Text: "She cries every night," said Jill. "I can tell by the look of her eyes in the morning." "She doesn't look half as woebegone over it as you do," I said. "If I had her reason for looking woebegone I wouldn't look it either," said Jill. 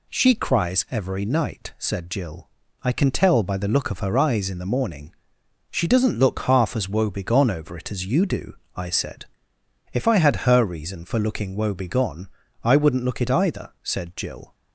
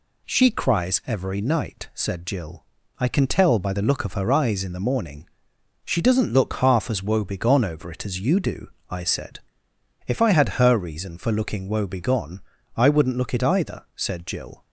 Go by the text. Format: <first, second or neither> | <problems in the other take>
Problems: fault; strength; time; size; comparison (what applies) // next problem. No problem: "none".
neither | pauses between "woebegone" and "I"; slight; the same in both